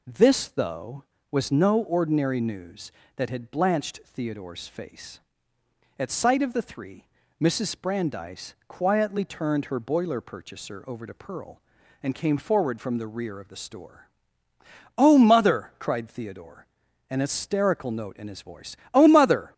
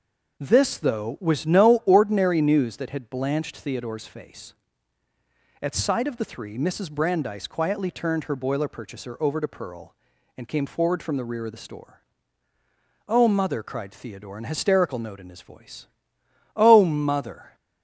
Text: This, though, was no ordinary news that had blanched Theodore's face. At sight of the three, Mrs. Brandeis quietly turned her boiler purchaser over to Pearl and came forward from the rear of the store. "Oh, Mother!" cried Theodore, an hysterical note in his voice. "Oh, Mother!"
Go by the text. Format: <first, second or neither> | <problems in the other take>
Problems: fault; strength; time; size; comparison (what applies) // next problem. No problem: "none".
neither | none